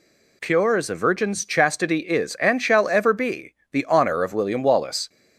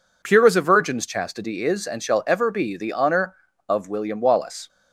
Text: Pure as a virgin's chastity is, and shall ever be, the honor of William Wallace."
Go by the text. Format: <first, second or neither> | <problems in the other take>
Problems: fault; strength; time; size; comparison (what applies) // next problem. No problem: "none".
neither | none